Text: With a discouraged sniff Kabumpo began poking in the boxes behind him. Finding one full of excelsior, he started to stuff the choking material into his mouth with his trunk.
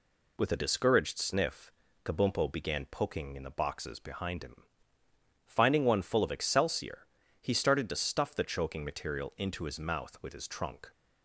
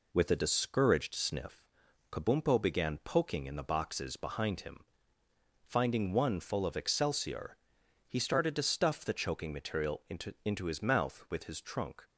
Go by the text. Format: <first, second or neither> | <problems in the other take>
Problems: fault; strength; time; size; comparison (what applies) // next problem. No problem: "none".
first | pauses between "sniff" and "Kabumpo"; noticeable; at 1.6 s; 0.48 s long; slight in the first // says "into" twice; at 10.4 s